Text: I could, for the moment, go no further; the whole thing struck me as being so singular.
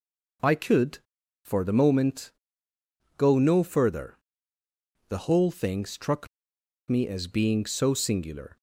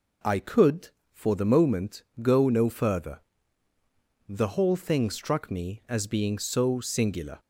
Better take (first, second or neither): second